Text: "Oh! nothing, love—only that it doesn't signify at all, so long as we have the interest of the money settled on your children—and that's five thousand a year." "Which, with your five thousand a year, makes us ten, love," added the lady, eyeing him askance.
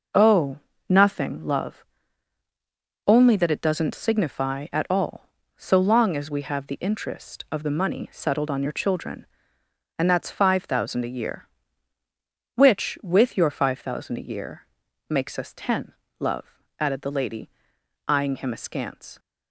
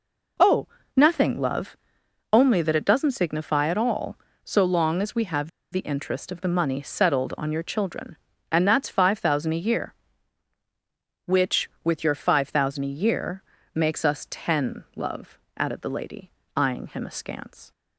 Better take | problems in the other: first | pauses between "have" and "the"; slight; at 5.4 s; 0.22 s long

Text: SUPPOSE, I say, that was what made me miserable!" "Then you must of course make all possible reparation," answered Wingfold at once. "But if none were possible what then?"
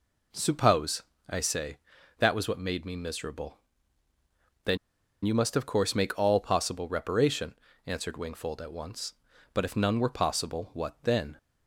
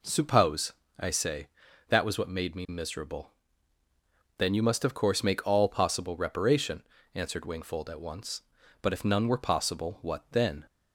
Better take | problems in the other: second | pauses between "Then" and "you"; noticeable; at 4.7 s; 0.47 s long

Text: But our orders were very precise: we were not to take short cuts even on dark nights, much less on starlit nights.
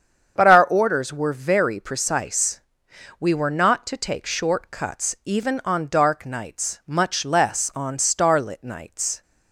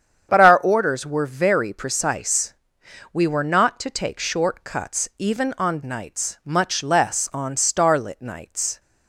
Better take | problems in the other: first | starts louder than the rest; strong; until 1.3 s; 8 dB; strong in the first // skips "dark"; at 5.8 s

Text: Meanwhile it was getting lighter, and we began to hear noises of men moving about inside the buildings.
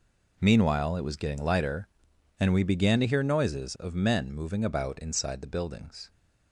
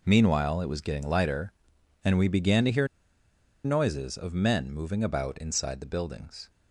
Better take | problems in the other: first | pauses between "hear" and "noises"; noticeable; at 2.8 s; 0.77 s long

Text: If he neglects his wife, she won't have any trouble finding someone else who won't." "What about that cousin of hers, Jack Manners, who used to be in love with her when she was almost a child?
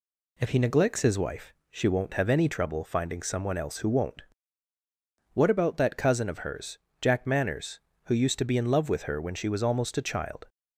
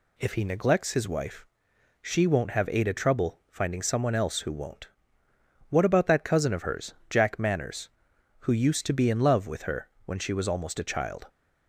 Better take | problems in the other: first | says "ada" for "any"; at 2.7 s // pauses between "her" and "when"; slight; at 9.8 s; 0.18 s long

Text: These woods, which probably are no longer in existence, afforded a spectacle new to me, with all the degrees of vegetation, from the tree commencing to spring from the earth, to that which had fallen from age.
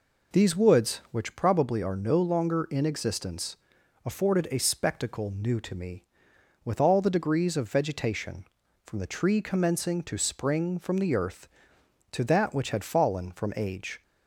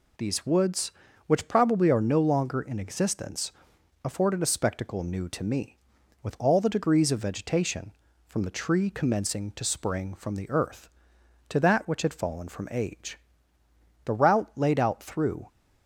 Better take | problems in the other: first | goes on to say "The route laid out through"; from 14.0 s on; 1.4 s long

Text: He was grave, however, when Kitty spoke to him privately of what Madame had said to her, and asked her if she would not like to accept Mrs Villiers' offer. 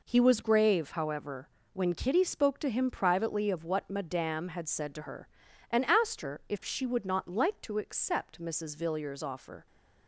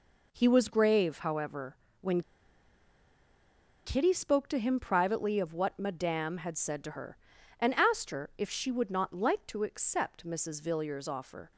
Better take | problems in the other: first | pauses between "when" and "Kitty"; strong; at 2.2 s; 1.6 s long

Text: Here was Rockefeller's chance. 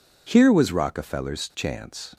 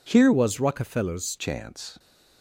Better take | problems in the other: first | changes voice from "was" to "Rockefeller's"; from 0.3 to 1.3 s; 1.0 s long

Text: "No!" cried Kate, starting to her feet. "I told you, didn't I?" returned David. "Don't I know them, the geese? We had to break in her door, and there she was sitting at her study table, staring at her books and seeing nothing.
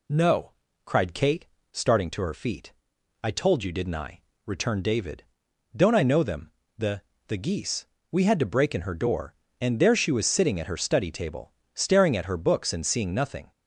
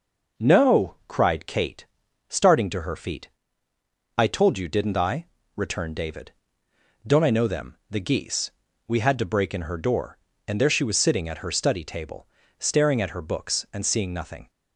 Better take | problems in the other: second | says "the" twice; at 7.2 s

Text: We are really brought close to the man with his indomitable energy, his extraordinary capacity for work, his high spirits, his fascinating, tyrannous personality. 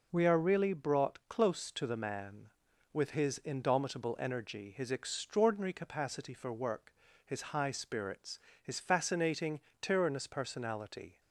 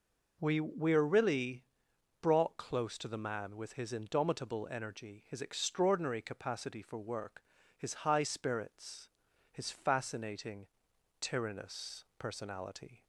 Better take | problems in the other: first | says "We" twice; at 0.6 s // pauses between "really" and "brought"; noticeable; at 1.6 s; 0.58 s long

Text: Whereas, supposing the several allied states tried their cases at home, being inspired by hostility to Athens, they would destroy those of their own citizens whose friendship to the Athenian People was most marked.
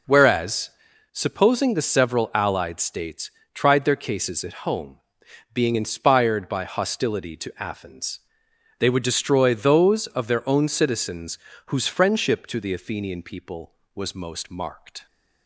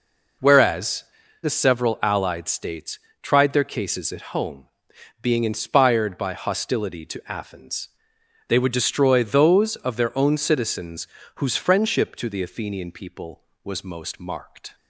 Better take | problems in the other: first | skips "supposing"; at 1.2 s // pauses between "states" and "tried"; slight; at 2.9 s; 0.24 s long; slight in the first // pauses between "citizens" and "whose"; slight; at 11.0 s; 0.28 s long; slight in the first

